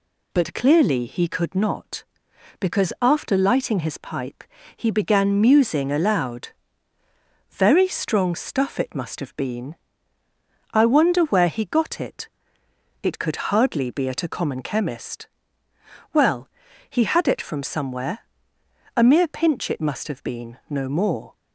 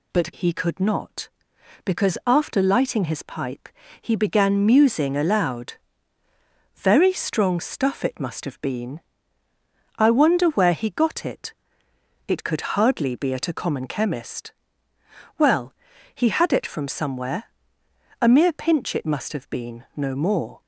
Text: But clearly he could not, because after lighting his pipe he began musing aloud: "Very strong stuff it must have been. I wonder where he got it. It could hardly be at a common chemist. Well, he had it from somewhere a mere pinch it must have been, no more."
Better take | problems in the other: first | skips "clearly"; at 0.3 s // pauses between "pipe" and "he"; slight; at 3.6 s; 0.34 s long; slight in the first // pauses between "somewhere" and "a"; noticeable; at 17.4 s; 0.78 s long; noticeable in the first

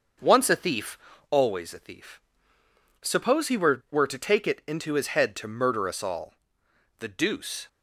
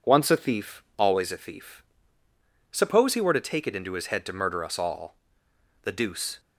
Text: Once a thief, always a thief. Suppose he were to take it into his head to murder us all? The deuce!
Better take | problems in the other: second | starts louder than the rest; until 1.5 s; 6.5 dB // says "were" twice; at 3.9 s

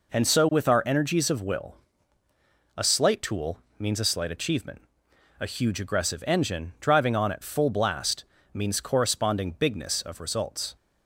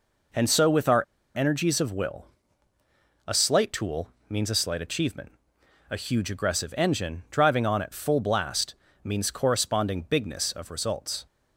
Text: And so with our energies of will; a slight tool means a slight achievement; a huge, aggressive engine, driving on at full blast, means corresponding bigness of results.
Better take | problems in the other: first | pauses between "our" and "energies"; slight; at 1.0 s; 0.32 s long // pauses between "tool" and "means"; slight; at 4.0 s; 0.20 s long; slight in the first

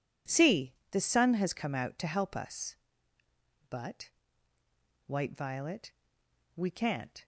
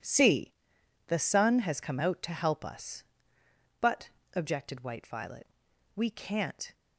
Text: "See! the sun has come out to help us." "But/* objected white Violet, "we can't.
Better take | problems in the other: second | skips "objected"; at 4.5 s

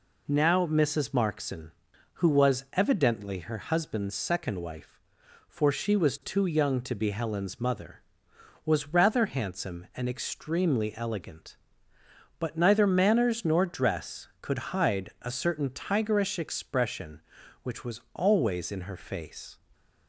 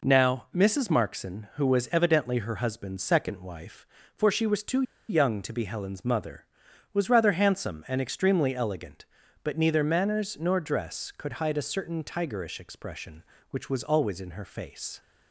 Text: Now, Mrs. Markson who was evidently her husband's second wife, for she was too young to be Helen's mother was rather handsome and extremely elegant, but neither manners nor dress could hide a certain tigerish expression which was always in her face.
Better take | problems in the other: first | pauses between "too" and "young"; slight; at 4.8 s; 0.26 s long

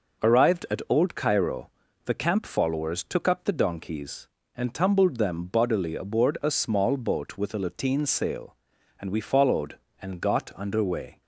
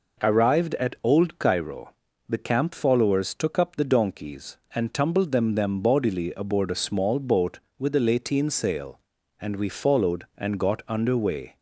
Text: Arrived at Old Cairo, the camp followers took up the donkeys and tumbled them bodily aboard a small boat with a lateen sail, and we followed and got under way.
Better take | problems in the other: first | says "them" twice; at 5.5 s

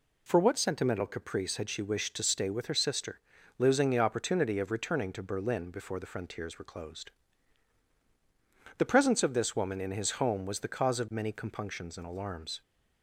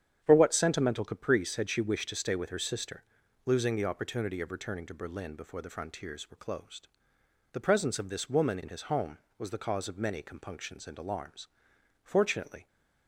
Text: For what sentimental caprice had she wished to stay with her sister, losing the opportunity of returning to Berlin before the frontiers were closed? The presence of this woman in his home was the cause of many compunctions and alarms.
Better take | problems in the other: first | starts louder than the rest; strong; until 1.2 s; 9 dB // goes on to say "Fortunately"; noticeable; from 12.0 s on; 0.64 s long

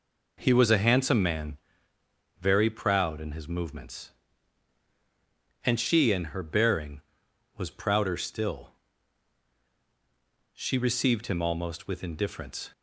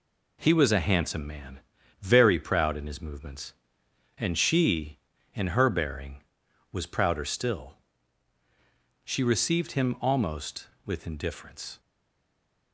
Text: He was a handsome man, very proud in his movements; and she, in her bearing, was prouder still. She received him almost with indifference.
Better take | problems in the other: first | stays silent after the last word; slight; from 11.7 s on; 1.0 s long

